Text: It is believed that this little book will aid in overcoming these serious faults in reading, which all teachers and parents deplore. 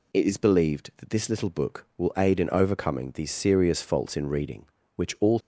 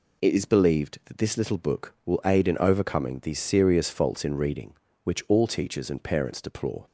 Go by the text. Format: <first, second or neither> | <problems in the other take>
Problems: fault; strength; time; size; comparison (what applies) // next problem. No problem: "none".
second | stops before "teachers and parents deplore"; at 5.3 s